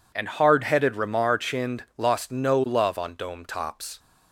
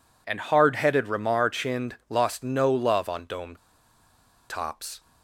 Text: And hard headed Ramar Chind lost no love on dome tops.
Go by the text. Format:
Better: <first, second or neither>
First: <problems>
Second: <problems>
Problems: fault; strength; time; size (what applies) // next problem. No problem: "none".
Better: first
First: none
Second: pauses between "dome" and "tops"; noticeable; at 3.5 s; 0.92 s long